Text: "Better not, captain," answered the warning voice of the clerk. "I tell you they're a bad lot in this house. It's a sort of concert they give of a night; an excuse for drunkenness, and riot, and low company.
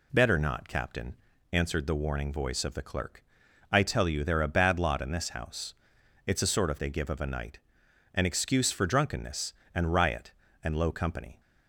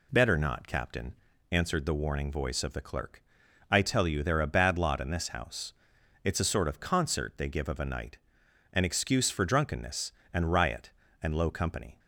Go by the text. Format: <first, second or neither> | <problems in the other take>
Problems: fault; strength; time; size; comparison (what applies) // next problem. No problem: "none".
second | skips "concert"; at 6.7 s